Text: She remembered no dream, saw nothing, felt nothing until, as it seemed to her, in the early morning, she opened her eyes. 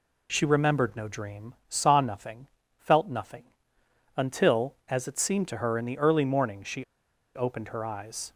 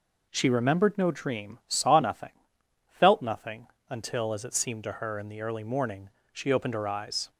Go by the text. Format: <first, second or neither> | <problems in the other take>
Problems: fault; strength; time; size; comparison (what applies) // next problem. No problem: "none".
second | pauses between "nothing" and "until"; noticeable; at 3.4 s; 0.72 s long; slight in the second // pauses between "she" and "opened"; noticeable; at 6.8 s; 0.50 s long